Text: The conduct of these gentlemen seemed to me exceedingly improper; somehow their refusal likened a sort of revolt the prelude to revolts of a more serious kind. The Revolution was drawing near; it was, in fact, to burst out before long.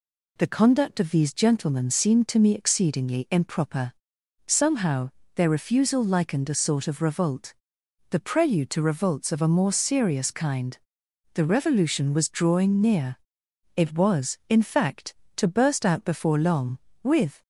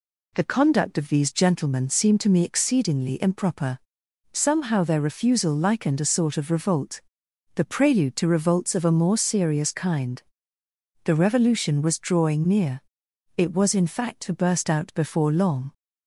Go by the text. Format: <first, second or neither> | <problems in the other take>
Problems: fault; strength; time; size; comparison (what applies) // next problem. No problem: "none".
second | pauses between "somehow" and "their"; slight; at 5.0 s; 0.26 s long // pauses between "revolt" and "the"; noticeable; at 7.5 s; 0.56 s long; noticeable in the second // goes on to say "With"; slight; from 17.0 s on; 0.40 s long